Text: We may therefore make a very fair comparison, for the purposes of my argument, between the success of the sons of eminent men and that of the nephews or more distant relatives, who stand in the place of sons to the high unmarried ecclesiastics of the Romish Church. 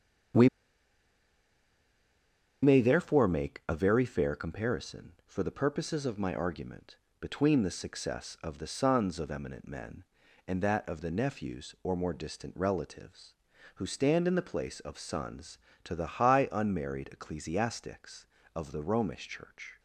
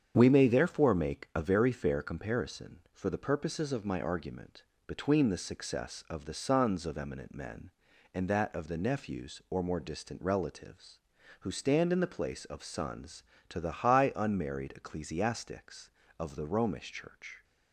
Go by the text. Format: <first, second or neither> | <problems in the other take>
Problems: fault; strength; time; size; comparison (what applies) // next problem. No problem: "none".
second | starts louder than the rest; strong; until 3.5 s; 8 dB; strong in the second // pauses between "We" and "may"; strong; at 0.4 s; 2.1 s long